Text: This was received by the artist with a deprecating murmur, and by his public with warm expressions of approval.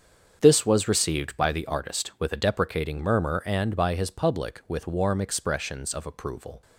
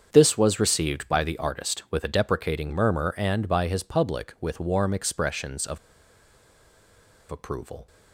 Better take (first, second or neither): first